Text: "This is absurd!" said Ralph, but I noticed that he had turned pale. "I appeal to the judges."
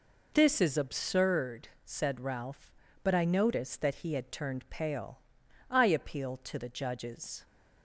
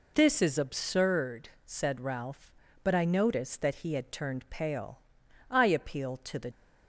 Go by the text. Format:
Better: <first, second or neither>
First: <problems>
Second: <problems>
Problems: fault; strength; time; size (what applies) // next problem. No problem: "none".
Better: first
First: none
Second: stops before "judges"; at 6.5 s